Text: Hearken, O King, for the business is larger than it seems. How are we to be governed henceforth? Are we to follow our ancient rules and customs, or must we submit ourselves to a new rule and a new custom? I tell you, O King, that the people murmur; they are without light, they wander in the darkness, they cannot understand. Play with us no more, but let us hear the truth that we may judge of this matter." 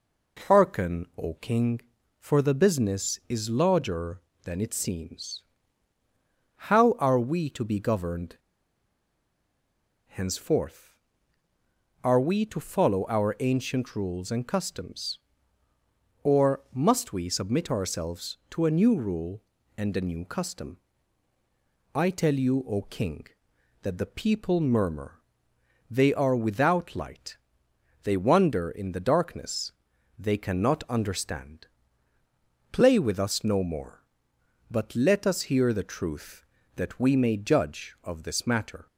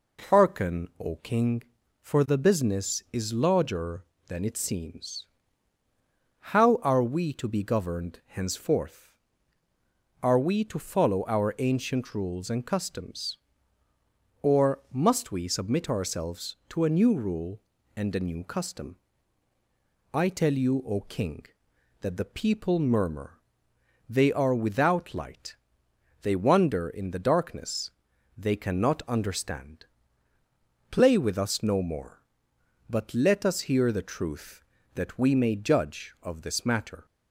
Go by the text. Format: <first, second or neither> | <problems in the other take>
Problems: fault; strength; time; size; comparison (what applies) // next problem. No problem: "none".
second | pauses between "governed" and "henceforth"; strong; at 8.3 s; 1.7 s long